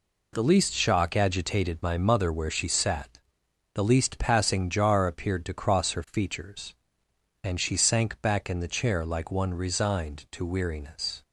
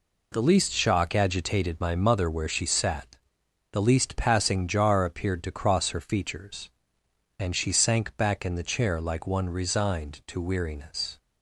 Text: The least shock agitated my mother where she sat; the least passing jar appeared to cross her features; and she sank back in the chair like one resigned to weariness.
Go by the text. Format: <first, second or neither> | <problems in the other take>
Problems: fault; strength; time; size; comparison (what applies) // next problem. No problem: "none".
neither | none